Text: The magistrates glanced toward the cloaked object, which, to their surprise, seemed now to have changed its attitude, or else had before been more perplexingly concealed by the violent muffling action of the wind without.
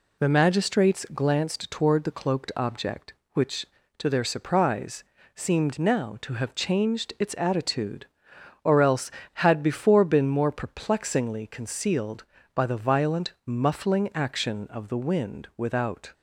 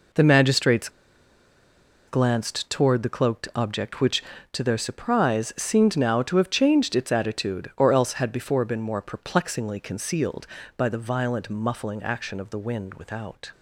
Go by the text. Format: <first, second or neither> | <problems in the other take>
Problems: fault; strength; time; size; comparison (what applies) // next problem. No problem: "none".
first | pauses between "magistrates" and "glanced"; at 0.8 s; 1.1 s long